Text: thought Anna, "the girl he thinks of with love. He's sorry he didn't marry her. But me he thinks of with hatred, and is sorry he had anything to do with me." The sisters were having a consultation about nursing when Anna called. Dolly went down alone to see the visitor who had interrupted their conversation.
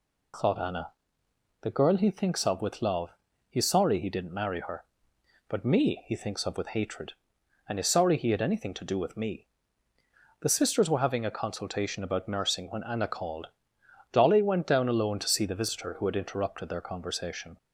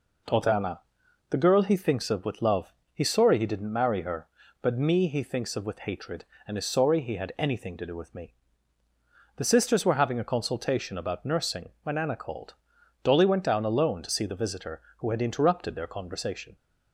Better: neither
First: none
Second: none

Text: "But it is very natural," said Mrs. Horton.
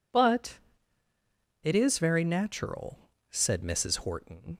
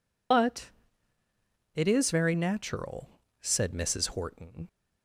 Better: first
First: pauses between "But" and "it"; at 0.5 s; 1.0 s long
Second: loses the start of "But"; at 0.3 s; 70 ms // pauses between "But" and "it"; at 0.6 s; 1.0 s long

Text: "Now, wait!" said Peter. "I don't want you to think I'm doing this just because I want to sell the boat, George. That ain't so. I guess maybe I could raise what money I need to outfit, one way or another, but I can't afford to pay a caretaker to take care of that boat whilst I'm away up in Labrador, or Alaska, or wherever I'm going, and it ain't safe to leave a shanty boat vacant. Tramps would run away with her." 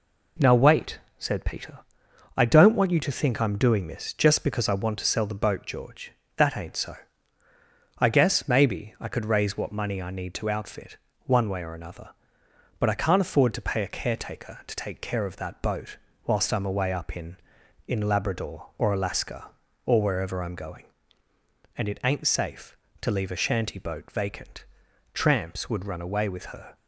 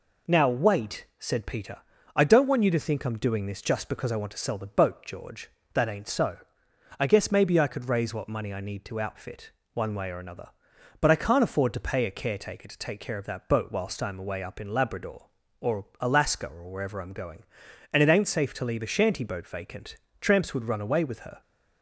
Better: second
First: pauses between "boat" and "whilst"; slight; at 15.9 s; 0.30 s long // says "in" twice; at 17.8 s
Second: none

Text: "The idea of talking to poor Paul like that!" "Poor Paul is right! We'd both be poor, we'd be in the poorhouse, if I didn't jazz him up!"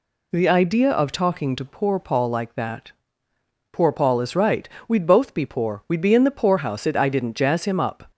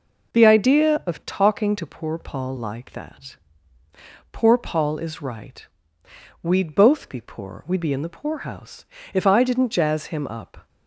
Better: second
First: says "it" for "if"; at 6.8 s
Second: none

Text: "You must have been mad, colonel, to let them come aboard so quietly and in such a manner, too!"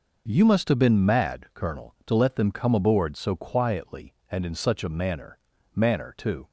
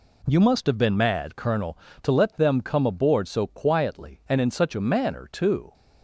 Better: second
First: says "manner" twice; at 5.7 s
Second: none

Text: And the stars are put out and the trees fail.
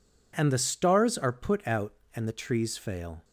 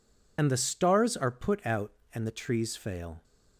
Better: first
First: none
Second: loses the start of "And"; at 0.3 s; 65 ms

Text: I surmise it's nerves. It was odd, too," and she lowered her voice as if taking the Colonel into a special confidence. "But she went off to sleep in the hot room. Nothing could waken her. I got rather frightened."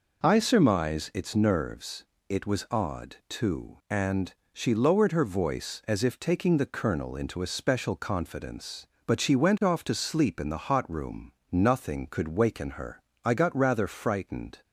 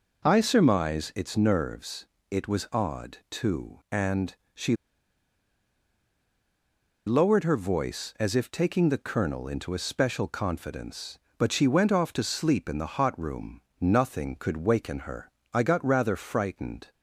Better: first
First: pauses between "and" and "she"; slight; at 4.3 s; 0.22 s long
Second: pauses between "and" and "she"; slight; at 4.3 s; 0.22 s long // pauses between "she" and "lowered"; strong; at 4.7 s; 2.3 s long

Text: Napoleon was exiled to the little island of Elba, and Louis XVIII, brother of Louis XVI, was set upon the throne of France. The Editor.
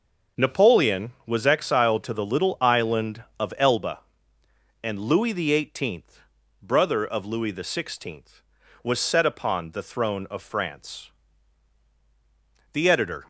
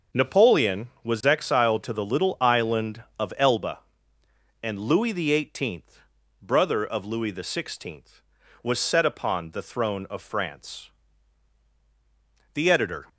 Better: neither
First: starts louder than the rest; until 1.5 s; 6.5 dB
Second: starts louder than the rest; until 1.3 s; 6.5 dB

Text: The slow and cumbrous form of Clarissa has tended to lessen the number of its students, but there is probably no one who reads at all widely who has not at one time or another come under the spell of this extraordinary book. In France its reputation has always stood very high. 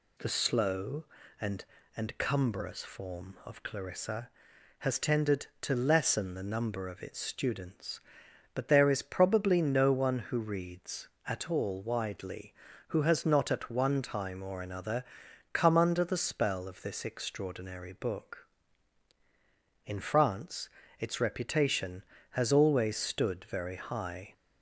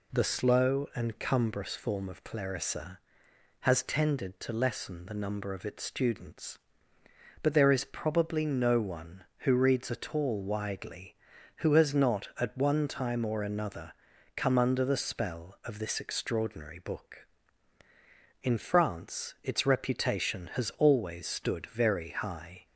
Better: second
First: says "and" twice; at 1.9 s // pauses between "another" and "come"; noticeable; at 15.0 s; 0.50 s long // pauses between "France" and "its"; slight; at 20.6 s; 0.30 s long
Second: pauses between "another" and "come"; at 13.9 s; 0.42 s long

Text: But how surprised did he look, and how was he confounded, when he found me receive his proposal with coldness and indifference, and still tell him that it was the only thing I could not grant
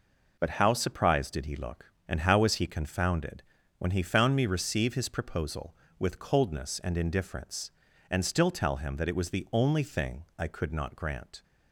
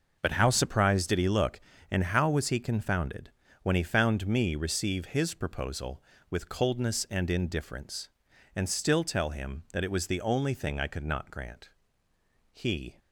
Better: first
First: none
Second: goes on to say "He"; slight; from 12.5 s on; 0.46 s long

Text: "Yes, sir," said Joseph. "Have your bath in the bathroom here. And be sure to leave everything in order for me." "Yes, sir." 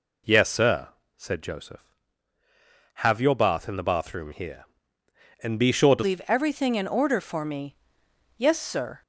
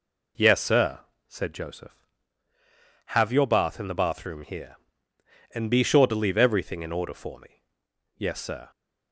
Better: second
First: changes voice at "leave"; from 6.0 s on; 3.0 s long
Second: none

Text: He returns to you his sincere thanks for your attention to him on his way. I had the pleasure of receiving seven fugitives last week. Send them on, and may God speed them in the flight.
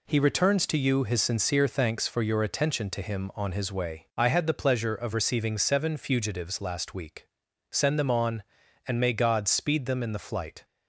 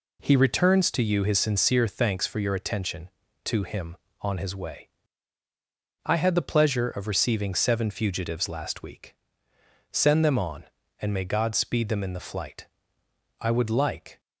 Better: first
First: none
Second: goes on to say "I would like"; noticeable; from 13.3 s on; 0.80 s long

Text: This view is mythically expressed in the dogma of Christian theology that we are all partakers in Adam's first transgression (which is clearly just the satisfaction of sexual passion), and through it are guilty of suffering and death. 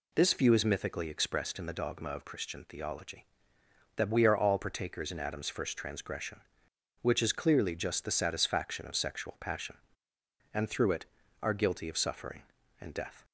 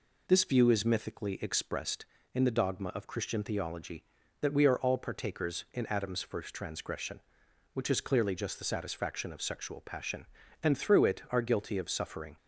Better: first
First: none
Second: stops before "and death"; at 12.3 s

